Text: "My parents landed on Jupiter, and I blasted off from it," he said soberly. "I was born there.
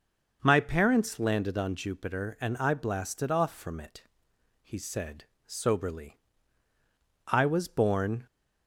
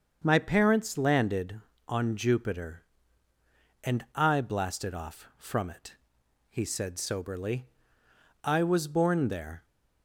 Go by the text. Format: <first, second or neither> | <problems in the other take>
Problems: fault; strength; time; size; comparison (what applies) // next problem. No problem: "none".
second | starts louder than the rest; until 1.4 s; 6 dB; also in the second // pauses between "said" and "soberly"; slight; at 5.2 s; 0.18 s long // stops before "there"; at 8.2 s